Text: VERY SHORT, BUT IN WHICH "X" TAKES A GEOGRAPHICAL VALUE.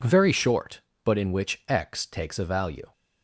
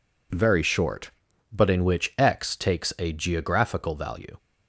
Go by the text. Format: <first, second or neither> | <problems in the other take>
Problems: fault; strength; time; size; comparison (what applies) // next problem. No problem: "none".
second | skips "GEOGRAPHICAL"; at 2.4 s